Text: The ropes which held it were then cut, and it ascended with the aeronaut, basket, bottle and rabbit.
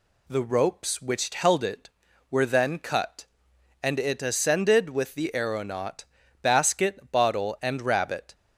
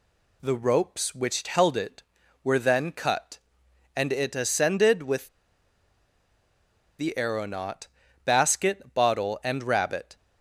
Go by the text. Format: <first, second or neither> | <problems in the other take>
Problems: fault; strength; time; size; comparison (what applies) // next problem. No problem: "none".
first | pauses between "with" and "the"; strong; at 5.2 s; 1.7 s long